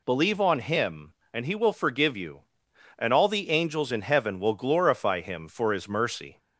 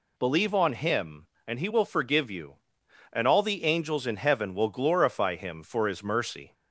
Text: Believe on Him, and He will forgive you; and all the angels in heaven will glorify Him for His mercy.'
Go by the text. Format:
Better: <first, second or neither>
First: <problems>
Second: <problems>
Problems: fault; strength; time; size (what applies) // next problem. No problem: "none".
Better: neither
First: none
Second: none